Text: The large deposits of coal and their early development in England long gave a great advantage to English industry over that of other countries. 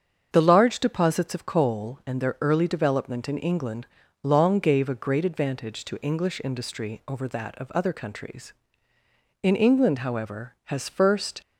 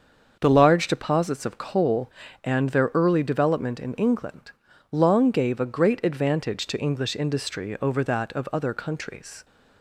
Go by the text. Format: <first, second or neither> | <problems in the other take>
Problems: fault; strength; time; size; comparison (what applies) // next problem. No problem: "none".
second | starts louder than the rest; strong; until 1.3 s; 7 dB; also in the second // pauses between "England" and "long"; slight; at 3.8 s; 0.34 s long; also in the second // goes on to say "In England however has first"; strong; from 9.4 s on; 1.9 s long